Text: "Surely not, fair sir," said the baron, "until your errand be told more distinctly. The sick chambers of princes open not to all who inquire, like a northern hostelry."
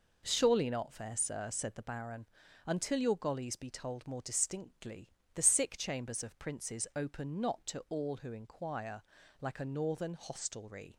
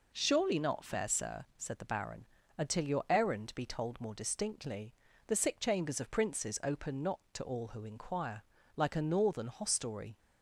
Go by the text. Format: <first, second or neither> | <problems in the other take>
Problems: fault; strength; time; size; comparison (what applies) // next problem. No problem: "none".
second | says "gollies" for "errand"; at 3.1 s